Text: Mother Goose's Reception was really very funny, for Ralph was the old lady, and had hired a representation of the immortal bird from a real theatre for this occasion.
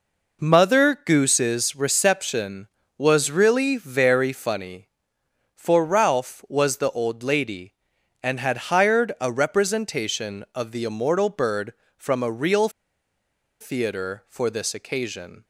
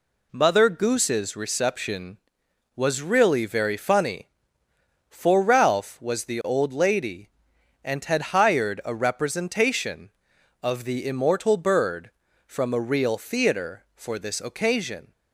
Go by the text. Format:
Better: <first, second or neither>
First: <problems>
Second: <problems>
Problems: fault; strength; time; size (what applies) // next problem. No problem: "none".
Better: second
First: pauses between "real" and "theatre"; noticeable; at 12.6 s; 0.91 s long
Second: none